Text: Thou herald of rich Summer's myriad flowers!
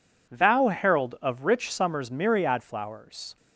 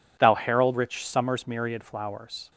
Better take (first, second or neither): first